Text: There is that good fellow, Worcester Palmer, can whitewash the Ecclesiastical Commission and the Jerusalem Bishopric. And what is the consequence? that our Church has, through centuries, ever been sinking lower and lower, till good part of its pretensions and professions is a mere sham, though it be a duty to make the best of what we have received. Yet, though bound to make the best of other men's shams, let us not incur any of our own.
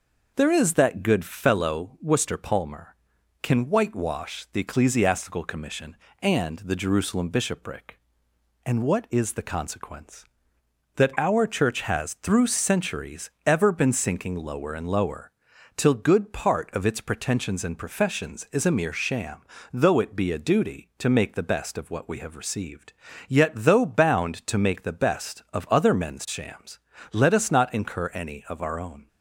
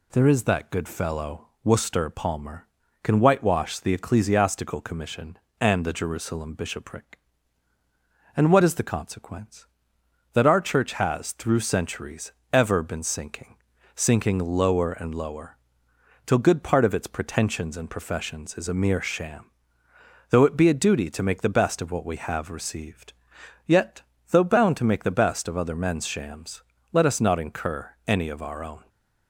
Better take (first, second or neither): first